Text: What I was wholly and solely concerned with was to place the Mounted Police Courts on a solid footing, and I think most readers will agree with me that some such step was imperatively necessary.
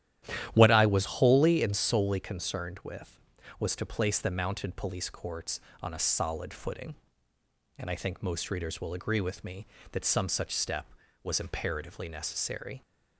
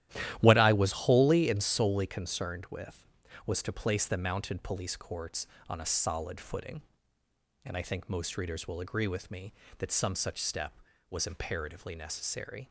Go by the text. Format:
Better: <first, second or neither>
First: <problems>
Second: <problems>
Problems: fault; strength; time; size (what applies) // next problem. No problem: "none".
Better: first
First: starts louder than the rest; strong; until 1.5 s; 11.5 dB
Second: gets quieter; strong; throughout; 9.5 dB // starts louder than the rest; strong; until 1.4 s; 12.5 dB